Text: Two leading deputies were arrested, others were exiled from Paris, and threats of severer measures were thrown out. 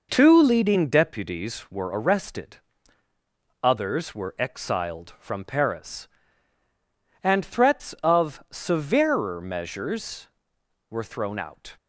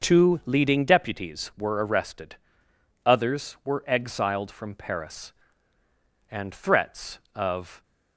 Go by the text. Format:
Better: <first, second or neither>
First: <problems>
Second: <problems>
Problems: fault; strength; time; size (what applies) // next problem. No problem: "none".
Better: first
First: none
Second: stops before "severer measures were thrown out"; at 7.8 s